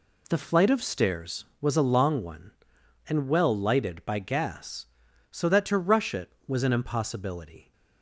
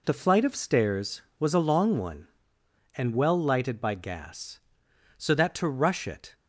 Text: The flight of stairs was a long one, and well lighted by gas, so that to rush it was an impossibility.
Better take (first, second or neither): first